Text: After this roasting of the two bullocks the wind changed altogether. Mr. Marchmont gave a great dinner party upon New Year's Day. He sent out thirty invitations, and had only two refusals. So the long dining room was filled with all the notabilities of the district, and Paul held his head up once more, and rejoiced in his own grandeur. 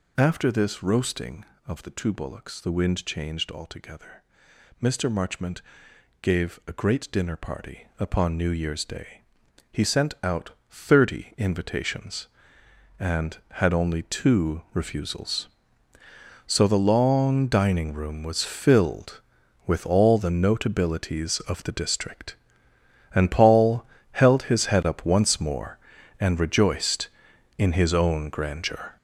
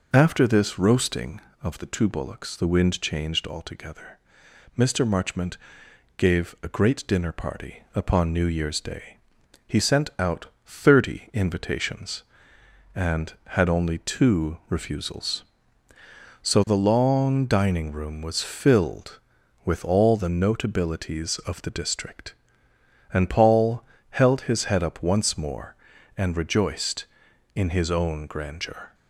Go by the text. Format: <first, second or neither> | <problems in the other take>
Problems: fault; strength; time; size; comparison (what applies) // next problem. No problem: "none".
second | gets louder; strong; throughout; 8.5 dB // pauses between "Marchmont" and "gave"; noticeable; at 5.5 s; 0.62 s long; noticeable in the second // pauses between "out" and "thirty"; slight; at 10.5 s; 0.18 s long; slight in the second // pauses between "Paul" and "held"; slight; at 23.8 s; 0.30 s long; slight in the second